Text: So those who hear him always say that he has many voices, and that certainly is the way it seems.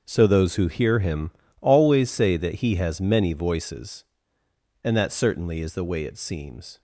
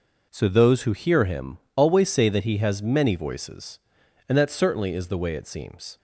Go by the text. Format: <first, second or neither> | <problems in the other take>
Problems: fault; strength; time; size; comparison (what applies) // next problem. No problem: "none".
second | gets quieter; strong; throughout; 13 dB // pauses between "him" and "always"; slight; at 1.2 s; 0.30 s long; slight in the second